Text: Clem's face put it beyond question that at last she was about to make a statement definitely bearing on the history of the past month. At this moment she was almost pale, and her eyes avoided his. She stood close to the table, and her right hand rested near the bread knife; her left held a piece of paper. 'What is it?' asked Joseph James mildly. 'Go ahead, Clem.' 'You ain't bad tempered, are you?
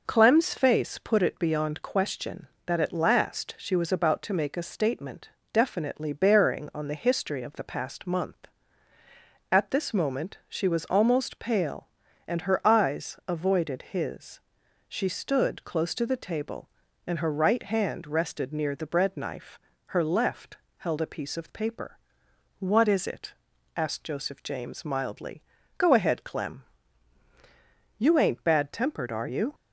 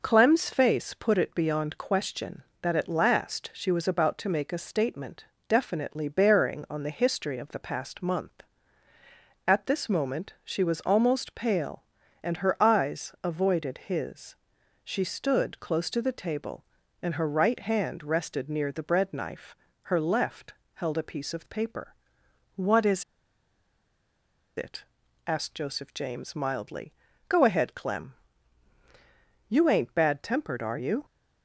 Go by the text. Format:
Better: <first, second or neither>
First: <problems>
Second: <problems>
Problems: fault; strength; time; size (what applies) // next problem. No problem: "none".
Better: first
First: pauses between "statement" and "definitely"; slight; at 5.3 s; 0.22 s long // pauses between "left" and "held"; slight; at 20.5 s; 0.20 s long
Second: pauses between "statement" and "definitely"; slight; at 5.2 s; 0.22 s long // pauses between "left" and "held"; slight; at 20.5 s; 0.20 s long // pauses between "is" and "it"; strong; at 23.0 s; 1.5 s long